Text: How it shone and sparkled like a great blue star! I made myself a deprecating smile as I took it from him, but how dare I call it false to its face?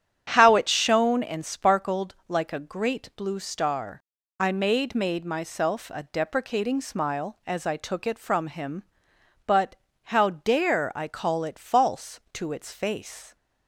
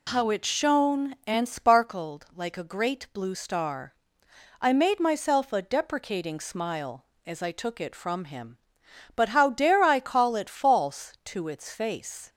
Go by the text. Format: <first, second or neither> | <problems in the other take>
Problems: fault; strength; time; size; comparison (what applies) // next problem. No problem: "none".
second | starts louder than the rest; strong; until 1.3 s; 9 dB // says "made" twice; at 4.9 s // pauses between "but" and "how"; slight; at 9.7 s; 0.28 s long